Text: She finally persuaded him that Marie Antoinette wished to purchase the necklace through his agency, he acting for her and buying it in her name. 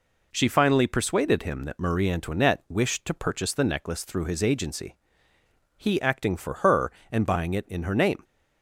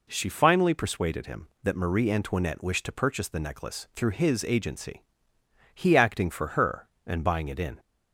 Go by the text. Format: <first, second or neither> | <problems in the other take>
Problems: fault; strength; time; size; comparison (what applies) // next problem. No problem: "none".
first | stops before "her name"; at 7.7 s